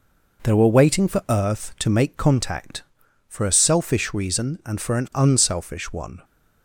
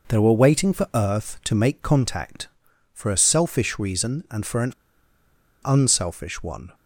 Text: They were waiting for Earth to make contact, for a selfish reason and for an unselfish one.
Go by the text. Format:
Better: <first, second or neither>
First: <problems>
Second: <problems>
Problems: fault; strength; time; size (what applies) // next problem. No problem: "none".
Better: first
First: none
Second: pauses between "an" and "unselfish"; noticeable; at 4.7 s; 0.92 s long